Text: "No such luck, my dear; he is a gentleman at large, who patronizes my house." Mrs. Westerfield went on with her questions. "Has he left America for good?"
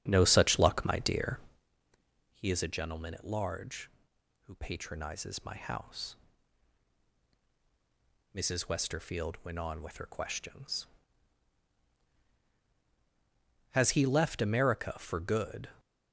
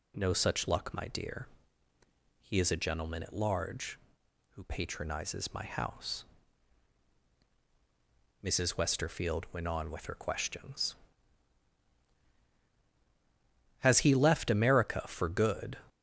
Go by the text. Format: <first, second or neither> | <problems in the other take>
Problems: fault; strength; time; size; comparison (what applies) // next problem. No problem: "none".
second | starts louder than the rest; strong; until 1.7 s; 9 dB